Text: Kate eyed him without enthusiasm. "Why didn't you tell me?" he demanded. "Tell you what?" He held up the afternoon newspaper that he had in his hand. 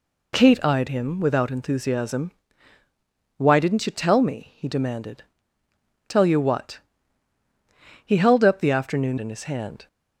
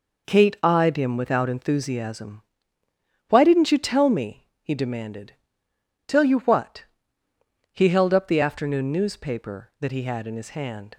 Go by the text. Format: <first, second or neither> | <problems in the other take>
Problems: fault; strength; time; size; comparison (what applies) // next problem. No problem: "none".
second | skips "newspaper that he had"; at 9.1 s